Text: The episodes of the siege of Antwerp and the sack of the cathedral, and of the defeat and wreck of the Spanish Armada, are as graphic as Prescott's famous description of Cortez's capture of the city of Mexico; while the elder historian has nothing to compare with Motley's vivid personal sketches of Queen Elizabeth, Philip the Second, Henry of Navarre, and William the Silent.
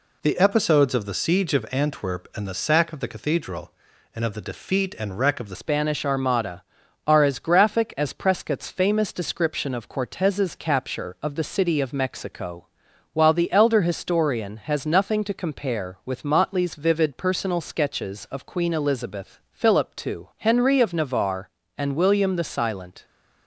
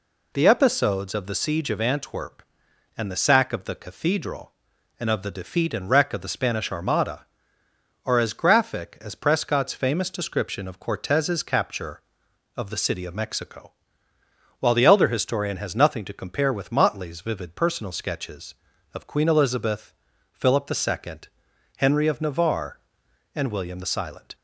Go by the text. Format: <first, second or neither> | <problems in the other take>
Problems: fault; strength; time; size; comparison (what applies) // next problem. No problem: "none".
second | changes voice at "Spanish"; from 5.5 s on; 17.5 s long